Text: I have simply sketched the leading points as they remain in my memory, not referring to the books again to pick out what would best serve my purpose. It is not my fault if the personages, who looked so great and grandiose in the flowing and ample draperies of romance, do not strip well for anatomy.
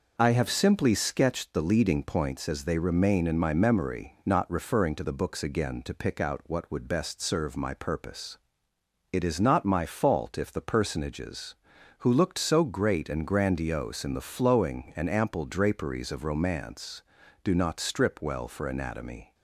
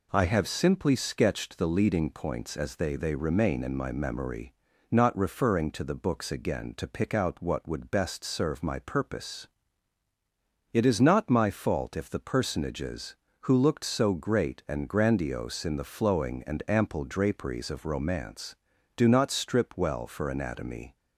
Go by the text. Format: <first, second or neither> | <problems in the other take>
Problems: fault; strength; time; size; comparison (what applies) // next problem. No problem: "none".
first | says "they" twice; at 2.9 s